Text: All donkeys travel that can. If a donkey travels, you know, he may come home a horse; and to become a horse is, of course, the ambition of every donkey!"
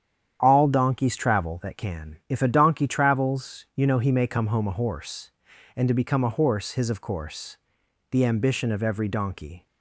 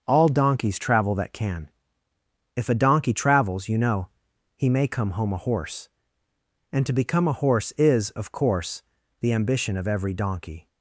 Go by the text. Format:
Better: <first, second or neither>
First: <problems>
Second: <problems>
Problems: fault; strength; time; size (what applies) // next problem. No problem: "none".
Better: second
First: starts louder than the rest; strong; until 1.4 s; 9.5 dB // says "his" for "is"; at 6.7 s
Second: starts louder than the rest; until 1.0 s; 6.5 dB